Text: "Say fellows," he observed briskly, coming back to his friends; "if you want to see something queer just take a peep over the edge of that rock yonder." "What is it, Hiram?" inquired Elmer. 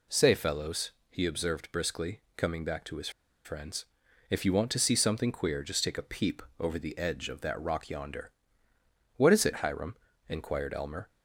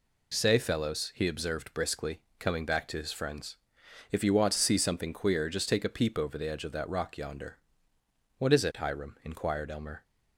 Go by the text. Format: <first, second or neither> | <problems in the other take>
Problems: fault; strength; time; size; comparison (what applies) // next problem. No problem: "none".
second | pauses between "his" and "friends"; slight; at 3.1 s; 0.34 s long // pauses between "peep" and "over"; slight; at 6.4 s; 0.18 s long